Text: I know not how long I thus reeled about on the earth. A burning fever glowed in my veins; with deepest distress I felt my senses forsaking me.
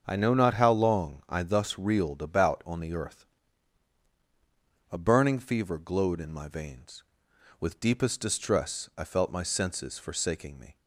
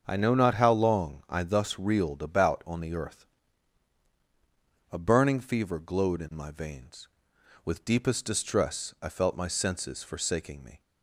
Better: neither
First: starts louder than the rest; until 1.0 s; 7 dB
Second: starts louder than the rest; until 1.0 s; 7 dB

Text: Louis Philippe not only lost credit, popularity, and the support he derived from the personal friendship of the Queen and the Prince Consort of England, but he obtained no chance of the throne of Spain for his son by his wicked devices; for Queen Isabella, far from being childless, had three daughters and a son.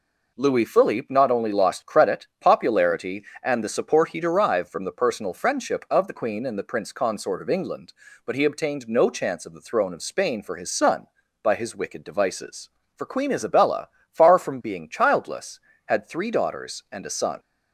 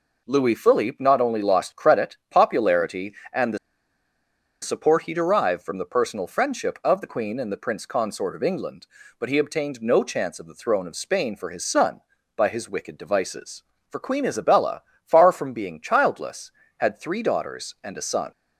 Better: first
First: none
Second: pauses between "the" and "support"; at 3.5 s; 1.0 s long

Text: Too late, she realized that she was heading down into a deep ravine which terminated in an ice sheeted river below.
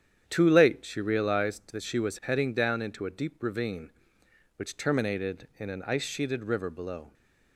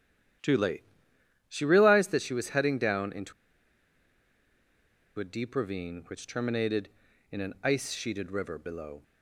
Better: first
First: starts louder than the rest; strong; until 1.2 s; 9 dB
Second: starts louder than the rest; strong; until 2.0 s; 10.5 dB // pauses between "into" and "a"; strong; at 3.3 s; 1.8 s long

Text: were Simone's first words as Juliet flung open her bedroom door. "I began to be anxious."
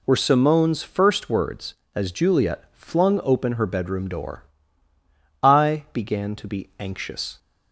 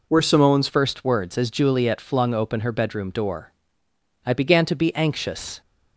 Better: first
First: none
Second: changes voice at "first"; from 0.6 s on; 5.0 s long

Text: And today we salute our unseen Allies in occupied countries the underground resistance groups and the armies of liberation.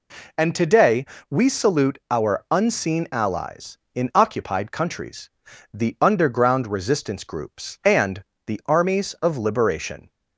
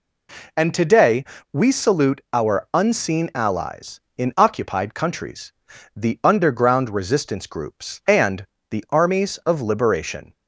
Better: neither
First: pauses between "today" and "we"; slight; at 1.0 s; 0.24 s long // pauses between "countries" and "the"; at 5.2 s; 0.44 s long // pauses between "and" and "the"; slight; at 8.2 s; 0.22 s long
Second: pauses between "today" and "we"; slight; at 1.2 s; 0.27 s long // pauses between "countries" and "the"; at 5.5 s; 0.44 s long // pauses between "and" and "the"; slight; at 8.4 s; 0.24 s long

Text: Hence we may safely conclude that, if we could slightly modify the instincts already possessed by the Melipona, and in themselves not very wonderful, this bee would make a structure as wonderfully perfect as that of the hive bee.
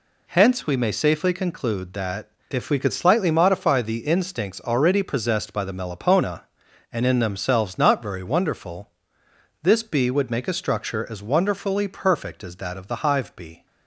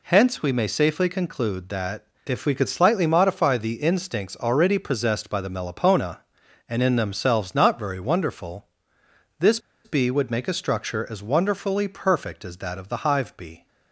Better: first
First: none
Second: pauses between "this" and "bee"; slight; at 9.5 s; 0.25 s long

